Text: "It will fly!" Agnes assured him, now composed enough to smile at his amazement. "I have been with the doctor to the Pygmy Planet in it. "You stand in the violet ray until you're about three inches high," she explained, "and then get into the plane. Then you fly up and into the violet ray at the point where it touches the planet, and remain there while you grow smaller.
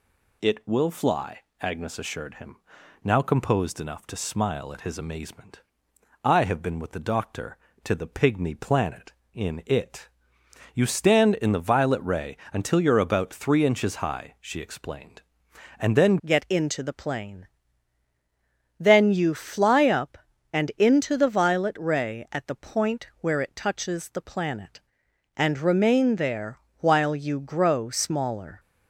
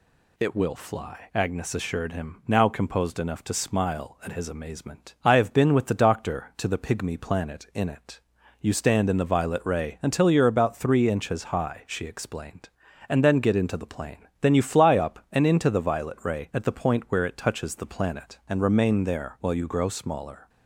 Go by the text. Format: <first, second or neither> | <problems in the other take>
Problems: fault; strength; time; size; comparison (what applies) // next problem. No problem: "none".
second | pauses between "ray" and "until"; slight; at 12.3 s; 0.16 s long // changes voice at "get"; from 16.2 s on; 12.3 s long // pauses between "there" and "while"; slight; at 26.5 s; 0.18 s long